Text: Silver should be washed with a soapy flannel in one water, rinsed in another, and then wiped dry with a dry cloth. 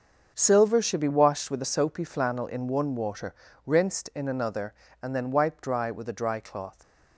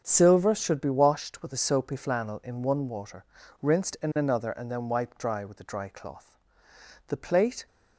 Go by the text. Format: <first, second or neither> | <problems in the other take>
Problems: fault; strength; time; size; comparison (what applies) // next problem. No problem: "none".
first | starts louder than the rest; until 1.0 s; 7 dB; also in the first // goes on to say "The plate"; from 7.0 s on; 0.58 s long